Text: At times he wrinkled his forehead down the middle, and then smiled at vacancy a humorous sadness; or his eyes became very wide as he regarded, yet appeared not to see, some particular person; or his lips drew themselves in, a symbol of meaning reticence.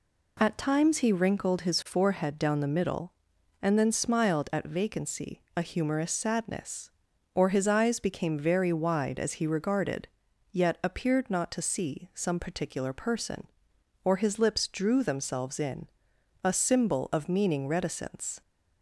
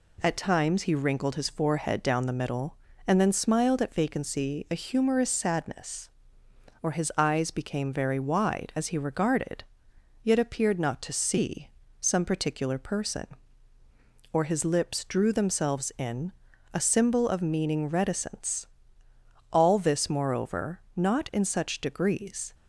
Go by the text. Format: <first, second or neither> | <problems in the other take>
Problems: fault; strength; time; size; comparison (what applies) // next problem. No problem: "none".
first | goes on to say "All this moreover not in such degrees"; strong; from 19.5 s on; 3.0 s long